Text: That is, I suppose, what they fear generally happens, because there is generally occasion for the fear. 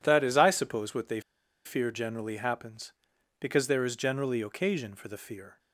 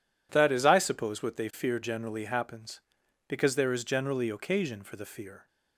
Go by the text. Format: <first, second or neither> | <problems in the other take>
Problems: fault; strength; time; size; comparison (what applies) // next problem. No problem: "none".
second | pauses between "they" and "fear"; at 1.2 s; 0.45 s long